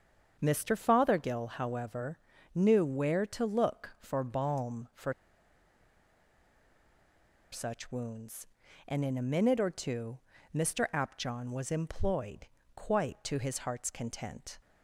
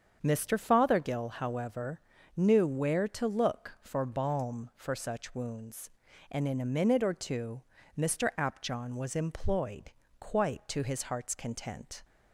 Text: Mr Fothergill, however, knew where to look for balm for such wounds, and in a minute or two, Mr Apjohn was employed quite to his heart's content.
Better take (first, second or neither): second